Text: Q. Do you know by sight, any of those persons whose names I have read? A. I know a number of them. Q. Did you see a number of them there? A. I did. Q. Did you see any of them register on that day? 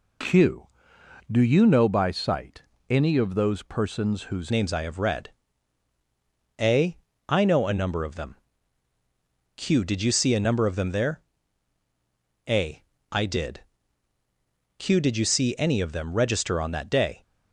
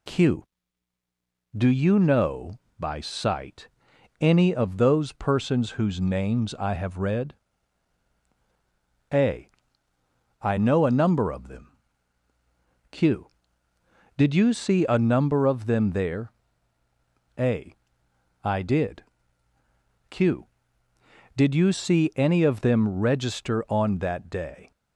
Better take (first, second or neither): second